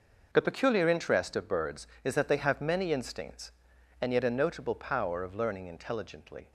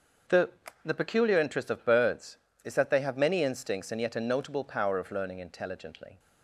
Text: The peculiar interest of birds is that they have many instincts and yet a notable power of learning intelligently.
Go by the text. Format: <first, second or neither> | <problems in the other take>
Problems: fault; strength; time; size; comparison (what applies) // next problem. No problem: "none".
first | starts louder than the rest; until 1.6 s; 6.5 dB // says "The" twice; at 0.8 s